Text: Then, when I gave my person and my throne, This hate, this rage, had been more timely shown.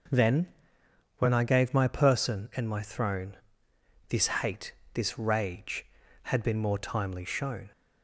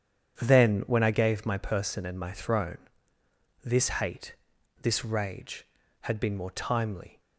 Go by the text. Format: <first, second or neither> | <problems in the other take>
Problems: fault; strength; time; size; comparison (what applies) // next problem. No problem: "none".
first | starts louder than the rest; strong; until 1.4 s; 8 dB // stops before "shown"; at 7.2 s